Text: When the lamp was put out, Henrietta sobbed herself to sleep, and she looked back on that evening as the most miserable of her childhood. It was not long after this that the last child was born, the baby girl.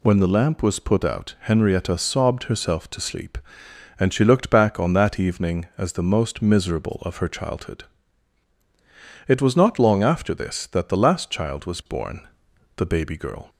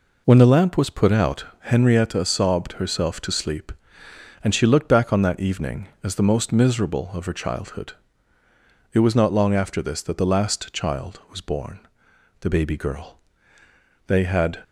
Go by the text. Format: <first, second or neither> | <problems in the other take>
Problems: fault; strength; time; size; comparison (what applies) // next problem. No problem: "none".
first | goes on to say "They had"; from 14.0 s on; 0.56 s long